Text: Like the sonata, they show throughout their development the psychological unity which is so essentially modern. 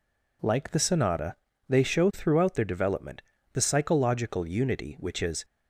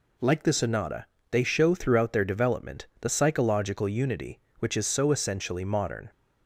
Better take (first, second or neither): second